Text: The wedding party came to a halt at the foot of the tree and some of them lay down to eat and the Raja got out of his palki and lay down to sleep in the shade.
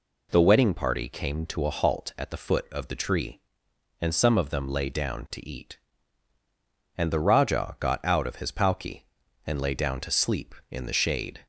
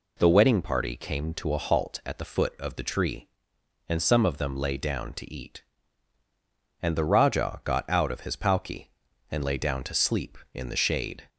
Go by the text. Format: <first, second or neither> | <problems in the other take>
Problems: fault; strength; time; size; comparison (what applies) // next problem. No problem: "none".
neither | none